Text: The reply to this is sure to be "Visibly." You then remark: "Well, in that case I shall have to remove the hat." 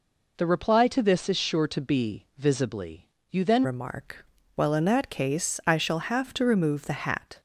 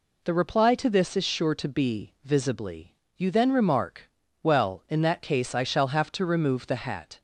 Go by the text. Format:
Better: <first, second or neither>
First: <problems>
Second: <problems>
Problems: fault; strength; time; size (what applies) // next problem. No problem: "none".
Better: second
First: changes voice at "remark"; from 3.6 s on; 3.7 s long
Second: none